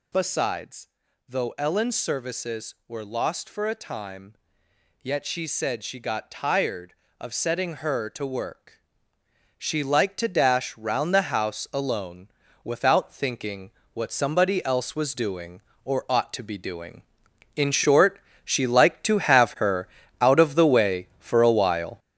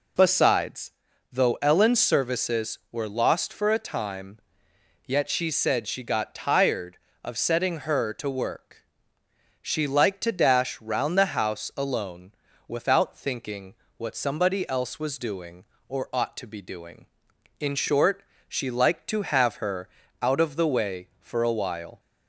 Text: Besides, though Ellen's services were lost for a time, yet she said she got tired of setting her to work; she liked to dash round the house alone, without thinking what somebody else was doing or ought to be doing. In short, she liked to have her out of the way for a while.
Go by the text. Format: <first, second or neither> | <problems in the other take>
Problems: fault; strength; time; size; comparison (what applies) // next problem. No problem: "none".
second | gets louder; strong; throughout; 7 dB // pauses between "thinking" and "what"; slight; at 13.7 s; 0.22 s long; slight in the second // pauses between "her" and "out"; slight; at 19.8 s; 0.32 s long; slight in the second